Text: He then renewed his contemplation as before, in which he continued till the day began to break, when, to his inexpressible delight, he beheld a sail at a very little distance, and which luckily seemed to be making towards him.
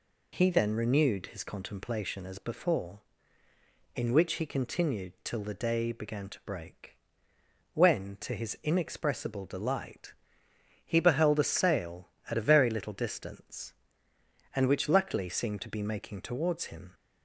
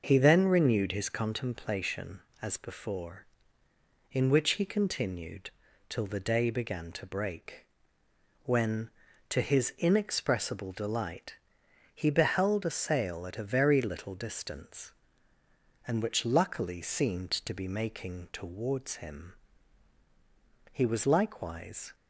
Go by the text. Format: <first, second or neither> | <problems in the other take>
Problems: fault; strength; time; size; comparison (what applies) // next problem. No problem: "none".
first | pauses between "continued" and "till"; at 5.4 s; 0.40 s long // goes on to say "He was likewise"; noticeable; from 20.7 s on; 1.2 s long